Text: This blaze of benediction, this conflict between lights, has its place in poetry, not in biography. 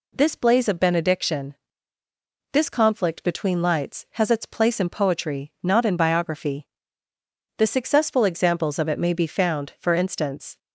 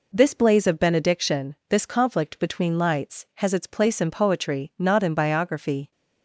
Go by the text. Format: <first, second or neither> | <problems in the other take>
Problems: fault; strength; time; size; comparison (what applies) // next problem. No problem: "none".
second | goes on to say "The successful examples of it may be found for instance"; strong; from 7.5 s on; 3.0 s long